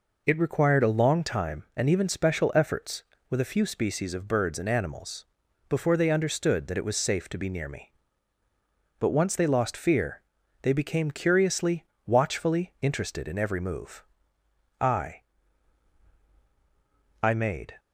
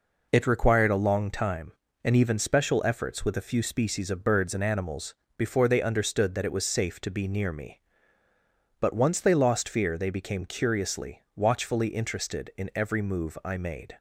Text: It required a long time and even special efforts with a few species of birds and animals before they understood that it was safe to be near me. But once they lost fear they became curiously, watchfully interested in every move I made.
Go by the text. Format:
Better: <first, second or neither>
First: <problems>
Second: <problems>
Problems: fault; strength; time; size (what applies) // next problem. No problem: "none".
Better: second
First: pauses between "animals" and "before"; at 5.2 s; 0.44 s long // pauses between "fear" and "they"; at 10.2 s; 0.42 s long // pauses between "move" and "I"; noticeable; at 14.0 s; 0.78 s long // says "I" twice; at 17.2 s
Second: pauses between "animals" and "before"; slight; at 5.1 s; 0.22 s long